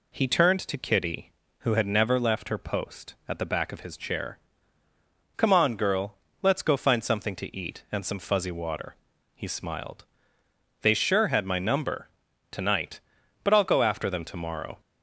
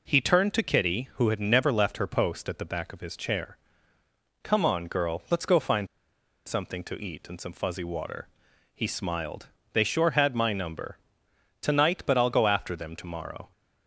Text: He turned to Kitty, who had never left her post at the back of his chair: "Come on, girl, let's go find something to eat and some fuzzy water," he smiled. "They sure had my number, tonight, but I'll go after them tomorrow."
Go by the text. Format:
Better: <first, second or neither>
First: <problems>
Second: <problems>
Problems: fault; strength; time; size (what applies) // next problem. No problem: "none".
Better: first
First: none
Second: pauses between "find" and "something"; noticeable; at 5.8 s; 0.60 s long